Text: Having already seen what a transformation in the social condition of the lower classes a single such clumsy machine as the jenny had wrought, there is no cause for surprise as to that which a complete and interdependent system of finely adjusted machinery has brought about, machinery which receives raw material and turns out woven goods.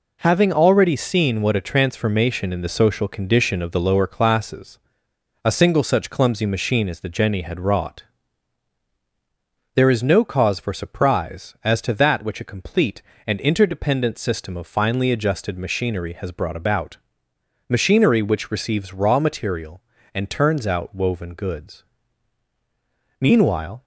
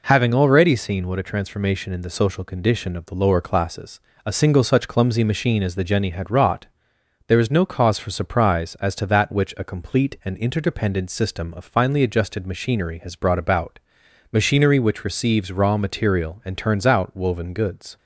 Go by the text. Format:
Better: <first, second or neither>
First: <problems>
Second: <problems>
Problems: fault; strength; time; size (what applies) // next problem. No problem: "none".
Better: second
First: pauses between "classes" and "a"; noticeable; at 4.7 s; 0.68 s long // goes on to say "Meanwhile"; noticeable; from 23.2 s on; 0.62 s long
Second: pauses between "classes" and "a"; slight; at 3.9 s; 0.24 s long